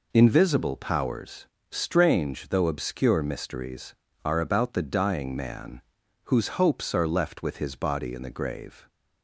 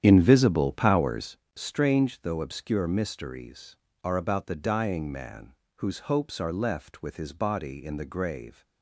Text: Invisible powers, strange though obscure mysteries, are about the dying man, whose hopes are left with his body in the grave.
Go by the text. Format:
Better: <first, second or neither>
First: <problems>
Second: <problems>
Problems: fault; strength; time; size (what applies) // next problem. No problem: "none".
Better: first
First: none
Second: starts louder than the rest; strong; until 1.3 s; 9.5 dB